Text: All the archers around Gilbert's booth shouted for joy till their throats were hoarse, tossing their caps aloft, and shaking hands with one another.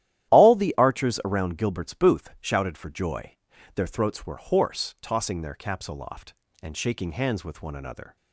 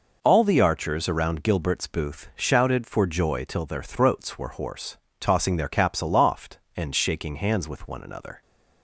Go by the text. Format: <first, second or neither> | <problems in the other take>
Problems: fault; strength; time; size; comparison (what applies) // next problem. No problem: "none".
second | starts louder than the rest; strong; until 1.3 s; 12.5 dB // skips "till"; at 3.5 s